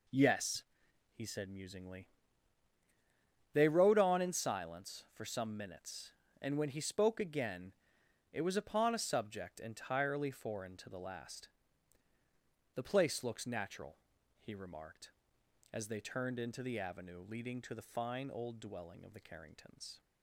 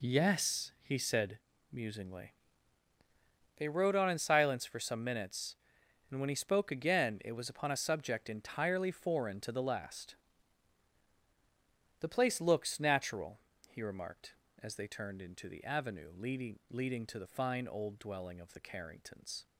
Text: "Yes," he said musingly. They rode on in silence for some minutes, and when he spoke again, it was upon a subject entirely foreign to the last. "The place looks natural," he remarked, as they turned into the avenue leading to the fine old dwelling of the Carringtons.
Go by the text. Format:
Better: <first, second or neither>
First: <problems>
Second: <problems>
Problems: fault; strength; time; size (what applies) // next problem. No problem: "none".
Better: first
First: none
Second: pauses between "said" and "musingly"; slight; at 1.3 s; 0.34 s long // says "leading" twice; at 16.7 s